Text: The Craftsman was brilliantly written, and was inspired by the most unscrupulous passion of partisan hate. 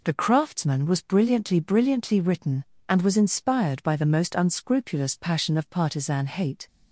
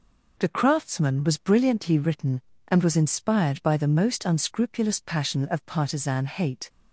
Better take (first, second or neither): second